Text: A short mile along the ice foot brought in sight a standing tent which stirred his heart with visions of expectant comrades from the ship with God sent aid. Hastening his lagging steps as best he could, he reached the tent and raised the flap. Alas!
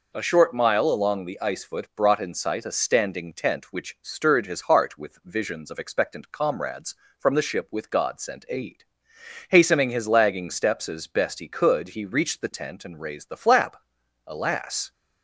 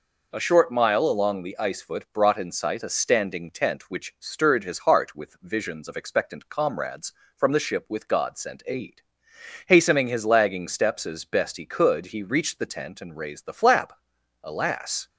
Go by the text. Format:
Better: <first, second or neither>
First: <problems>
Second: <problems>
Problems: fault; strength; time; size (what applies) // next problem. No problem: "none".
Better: neither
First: none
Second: none